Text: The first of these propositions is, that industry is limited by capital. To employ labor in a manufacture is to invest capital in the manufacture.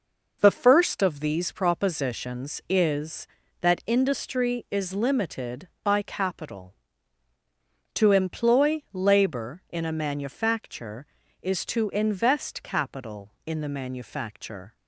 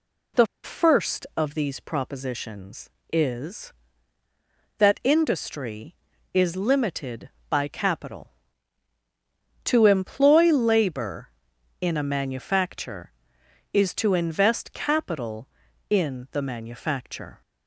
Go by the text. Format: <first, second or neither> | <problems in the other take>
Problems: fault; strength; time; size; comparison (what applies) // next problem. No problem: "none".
first | pauses between "The" and "first"; slight; at 0.4 s; 0.19 s long